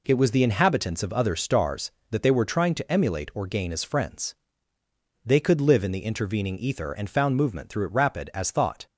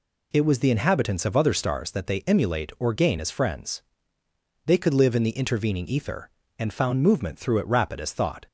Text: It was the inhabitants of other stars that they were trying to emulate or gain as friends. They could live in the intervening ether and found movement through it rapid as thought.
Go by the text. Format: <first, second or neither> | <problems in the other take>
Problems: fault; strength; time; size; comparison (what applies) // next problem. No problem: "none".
first | skips "were trying to"; at 2.2 s